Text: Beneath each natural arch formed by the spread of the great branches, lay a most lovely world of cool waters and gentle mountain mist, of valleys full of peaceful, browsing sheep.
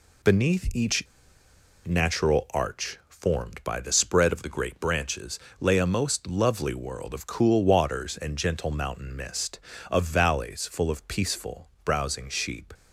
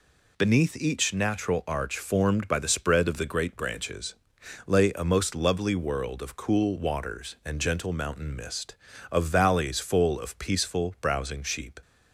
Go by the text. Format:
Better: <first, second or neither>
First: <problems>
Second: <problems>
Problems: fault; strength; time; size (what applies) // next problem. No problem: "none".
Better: second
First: pauses between "each" and "natural"; noticeable; at 1.0 s; 0.81 s long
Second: none